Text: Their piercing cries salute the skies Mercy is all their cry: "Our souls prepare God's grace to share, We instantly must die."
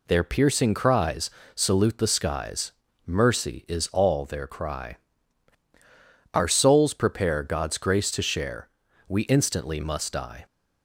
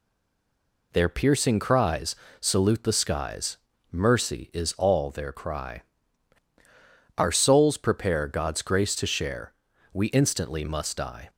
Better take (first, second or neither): first